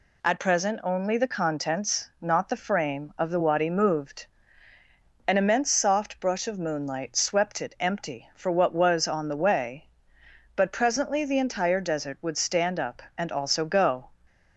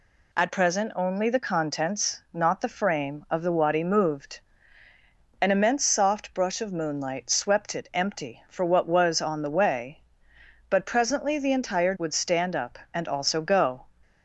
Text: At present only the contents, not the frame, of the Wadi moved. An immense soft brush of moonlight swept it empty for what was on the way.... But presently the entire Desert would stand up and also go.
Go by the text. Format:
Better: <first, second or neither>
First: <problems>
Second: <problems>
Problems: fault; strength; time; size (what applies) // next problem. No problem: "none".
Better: first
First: none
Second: skips "Desert"; at 11.9 s